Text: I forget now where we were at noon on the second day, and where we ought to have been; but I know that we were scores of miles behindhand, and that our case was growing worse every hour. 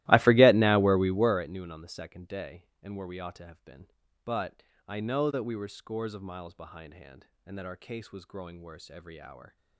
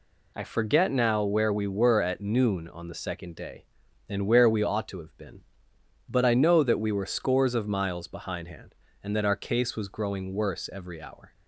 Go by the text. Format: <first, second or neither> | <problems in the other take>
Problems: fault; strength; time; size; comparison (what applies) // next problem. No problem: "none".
second | starts louder than the rest; strong; until 1.4 s; 17 dB // pauses between "but" and "I"; slight; at 4.6 s; 0.24 s long